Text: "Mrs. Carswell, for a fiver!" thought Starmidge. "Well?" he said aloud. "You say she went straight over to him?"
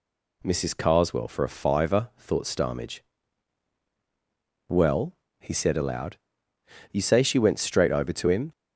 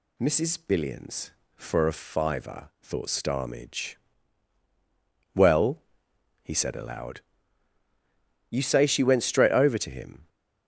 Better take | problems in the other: first | says "Billions" for "Carswell"; at 0.5 s

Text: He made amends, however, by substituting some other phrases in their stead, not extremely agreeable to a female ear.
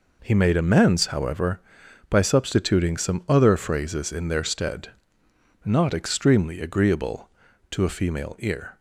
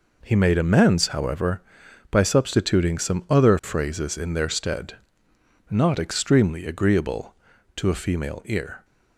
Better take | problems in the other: neither | none

